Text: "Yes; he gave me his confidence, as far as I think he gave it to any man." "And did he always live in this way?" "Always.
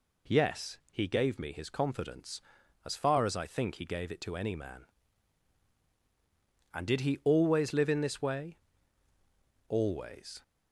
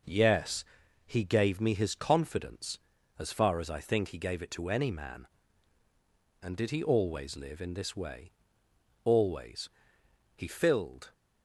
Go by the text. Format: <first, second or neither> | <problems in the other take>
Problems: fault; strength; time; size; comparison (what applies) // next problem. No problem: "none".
first | goes on to say "He filled"; noticeable; from 10.3 s on; 0.76 s long